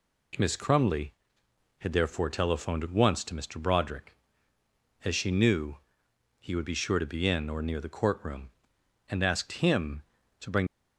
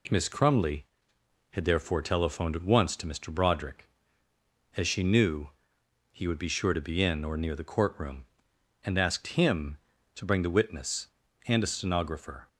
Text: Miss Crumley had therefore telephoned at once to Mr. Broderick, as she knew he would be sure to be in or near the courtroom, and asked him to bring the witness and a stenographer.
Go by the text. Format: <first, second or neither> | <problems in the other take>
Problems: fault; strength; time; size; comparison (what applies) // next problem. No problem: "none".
second | pauses between "knew" and "he"; noticeable; at 5.7 s; 0.64 s long; noticeable in the second // stops before "the witness and a stenographer"; at 10.6 s